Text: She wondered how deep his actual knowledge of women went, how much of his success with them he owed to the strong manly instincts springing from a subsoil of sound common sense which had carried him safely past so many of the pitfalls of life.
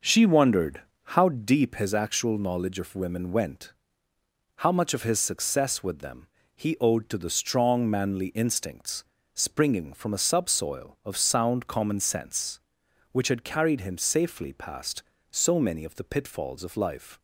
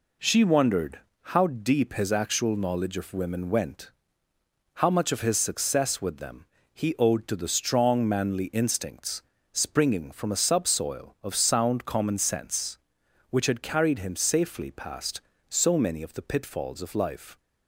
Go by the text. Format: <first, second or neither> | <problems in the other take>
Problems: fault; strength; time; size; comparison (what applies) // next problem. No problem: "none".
second | starts louder than the rest; noticeable; until 1.8 s; 5.5 dB // pauses between "wondered" and "how"; slight; at 0.8 s; 0.22 s long; slight in the second // pauses between "them" and "he"; slight; at 6.2 s; 0.30 s long; slight in the second // pauses between "instincts" and "springing"; slight; at 9.0 s; 0.32 s long; slight in the second